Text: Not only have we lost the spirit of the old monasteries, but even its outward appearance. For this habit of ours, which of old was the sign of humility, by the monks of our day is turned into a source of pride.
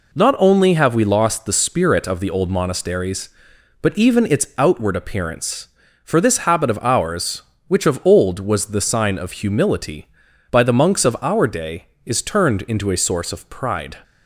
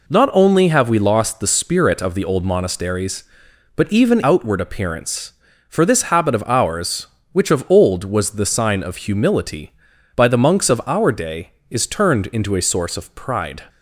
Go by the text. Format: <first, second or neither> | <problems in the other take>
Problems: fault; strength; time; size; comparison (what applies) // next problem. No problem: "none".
first | skips "its"; at 4.2 s